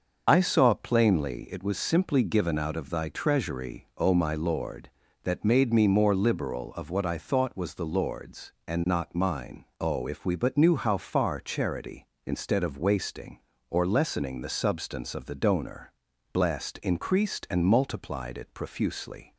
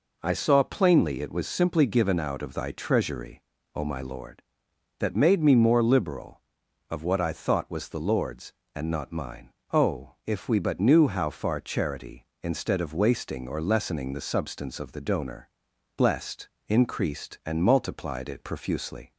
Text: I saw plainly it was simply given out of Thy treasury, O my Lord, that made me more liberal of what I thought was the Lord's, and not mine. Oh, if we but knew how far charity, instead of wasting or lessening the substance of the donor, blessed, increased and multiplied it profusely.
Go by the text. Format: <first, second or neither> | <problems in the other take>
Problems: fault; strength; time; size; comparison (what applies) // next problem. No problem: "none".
second | loses the start of "I"; at 0.2 s; 50 ms // starts louder than the rest; until 1.2 s; 6.5 dB